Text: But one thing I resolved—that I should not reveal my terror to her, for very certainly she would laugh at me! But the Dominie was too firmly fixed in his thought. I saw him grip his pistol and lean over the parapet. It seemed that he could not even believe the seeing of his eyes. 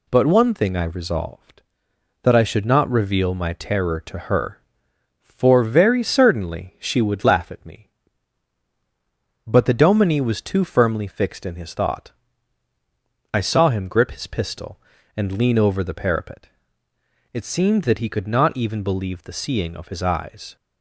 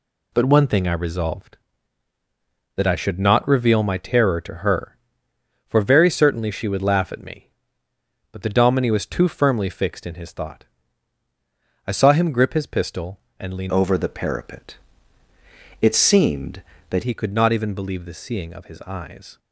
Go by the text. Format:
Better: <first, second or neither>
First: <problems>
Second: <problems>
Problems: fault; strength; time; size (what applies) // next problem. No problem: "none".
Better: first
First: none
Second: changes voice from "over" to "that"; from 13.6 to 17.0 s; 3.4 s long